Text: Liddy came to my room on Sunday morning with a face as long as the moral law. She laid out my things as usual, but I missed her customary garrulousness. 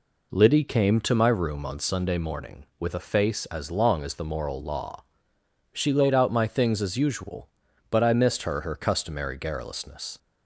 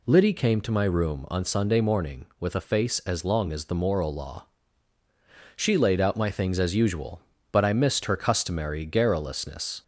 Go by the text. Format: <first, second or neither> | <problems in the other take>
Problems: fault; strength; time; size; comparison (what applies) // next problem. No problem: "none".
second | says "her" twice; at 8.5 s